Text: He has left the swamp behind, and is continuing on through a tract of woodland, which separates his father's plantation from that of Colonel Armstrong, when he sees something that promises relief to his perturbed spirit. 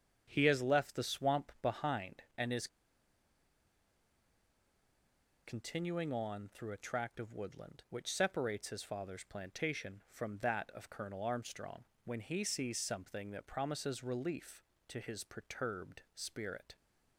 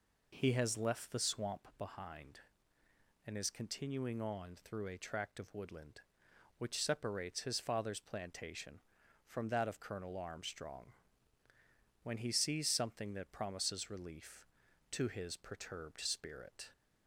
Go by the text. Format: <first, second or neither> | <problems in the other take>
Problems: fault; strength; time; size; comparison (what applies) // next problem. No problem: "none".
second | starts louder than the rest; strong; until 1.3 s; 8 dB // pauses between "is" and "continuing"; strong; at 2.6 s; 2.7 s long